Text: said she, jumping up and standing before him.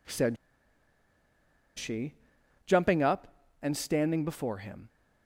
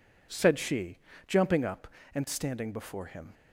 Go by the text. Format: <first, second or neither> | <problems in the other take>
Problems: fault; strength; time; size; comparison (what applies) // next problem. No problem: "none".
second | pauses between "said" and "she"; strong; at 0.3 s; 1.4 s long